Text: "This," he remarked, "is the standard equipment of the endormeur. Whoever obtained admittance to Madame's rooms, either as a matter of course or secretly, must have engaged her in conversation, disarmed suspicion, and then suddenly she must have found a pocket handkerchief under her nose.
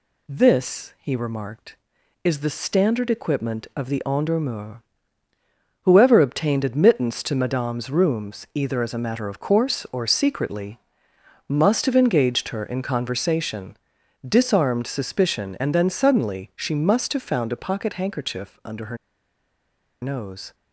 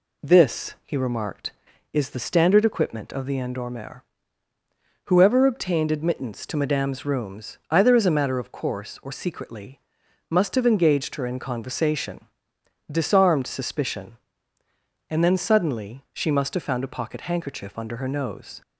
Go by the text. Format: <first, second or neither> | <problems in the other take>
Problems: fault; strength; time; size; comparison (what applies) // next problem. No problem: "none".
second | pauses between "her" and "nose"; at 18.9 s; 1.0 s long